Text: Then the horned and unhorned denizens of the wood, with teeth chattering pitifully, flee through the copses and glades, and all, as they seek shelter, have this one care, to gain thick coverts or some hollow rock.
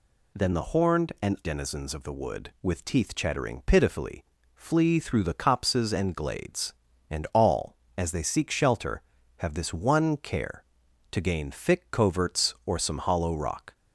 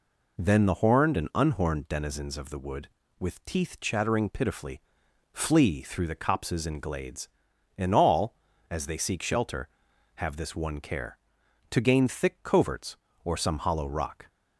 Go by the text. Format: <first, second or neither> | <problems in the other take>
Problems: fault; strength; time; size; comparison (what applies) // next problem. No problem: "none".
second | skips "unhorned"; at 1.4 s